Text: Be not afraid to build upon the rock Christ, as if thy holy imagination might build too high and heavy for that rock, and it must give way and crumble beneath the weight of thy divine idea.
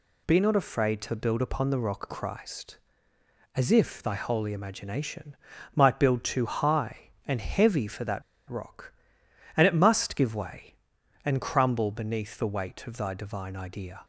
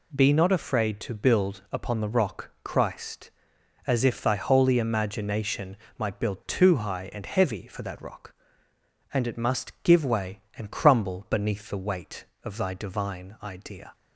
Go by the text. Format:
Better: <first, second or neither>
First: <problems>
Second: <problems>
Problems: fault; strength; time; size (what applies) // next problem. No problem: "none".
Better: second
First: pauses between "imagination" and "might"; at 5.3 s; 0.38 s long // pauses between "that" and "rock"; slight; at 8.2 s; 0.26 s long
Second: pauses between "imagination" and "might"; slight; at 5.7 s; 0.22 s long